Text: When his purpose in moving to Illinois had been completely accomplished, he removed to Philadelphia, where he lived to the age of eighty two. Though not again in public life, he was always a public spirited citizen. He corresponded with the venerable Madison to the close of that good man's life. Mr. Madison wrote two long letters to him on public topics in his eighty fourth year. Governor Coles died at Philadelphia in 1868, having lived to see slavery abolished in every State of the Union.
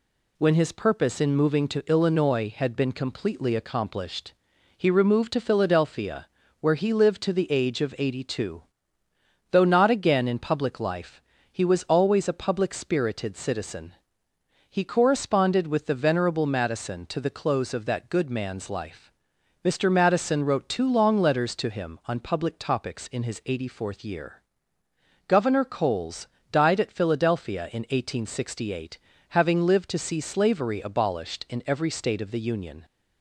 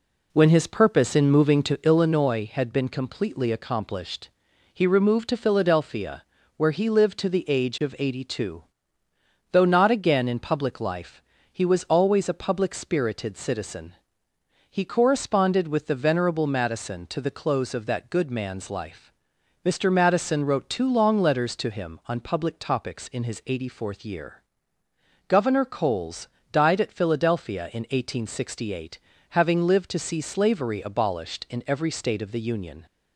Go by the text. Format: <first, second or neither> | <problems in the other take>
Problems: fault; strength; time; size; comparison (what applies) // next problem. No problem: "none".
first | starts louder than the rest; slight; until 2.1 s; 3 dB // pauses between "Coles" and "died"; slight; at 26.2 s; 0.26 s long; slight in the first